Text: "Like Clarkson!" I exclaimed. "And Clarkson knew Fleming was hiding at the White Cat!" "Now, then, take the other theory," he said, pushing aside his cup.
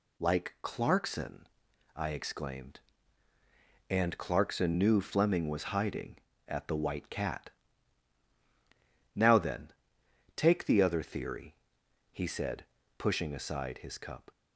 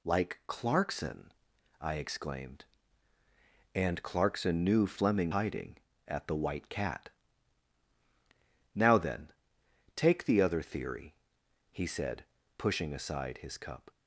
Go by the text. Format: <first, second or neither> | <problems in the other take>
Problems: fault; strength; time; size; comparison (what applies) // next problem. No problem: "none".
first | skips "was"; at 5.3 s